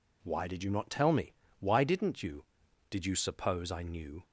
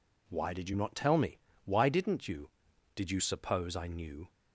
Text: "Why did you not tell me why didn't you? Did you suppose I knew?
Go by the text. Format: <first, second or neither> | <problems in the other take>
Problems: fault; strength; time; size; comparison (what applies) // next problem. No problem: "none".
neither | pauses between "me" and "why"; slight; the same in both